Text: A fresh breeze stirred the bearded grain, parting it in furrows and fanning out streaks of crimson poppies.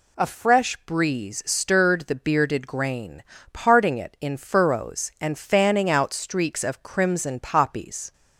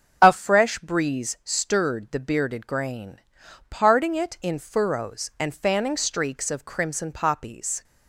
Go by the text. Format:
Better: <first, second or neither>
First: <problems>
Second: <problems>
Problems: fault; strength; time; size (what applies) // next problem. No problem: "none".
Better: first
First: none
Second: starts louder than the rest; until 1.2 s; 6.5 dB // skips "out"; at 5.9 s